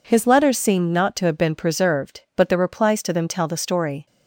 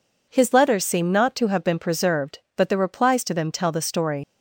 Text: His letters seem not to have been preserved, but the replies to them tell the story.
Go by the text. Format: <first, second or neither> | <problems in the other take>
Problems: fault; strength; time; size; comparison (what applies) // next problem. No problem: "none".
first | leaves "story" unfinished; at 4.2 s; 105 ms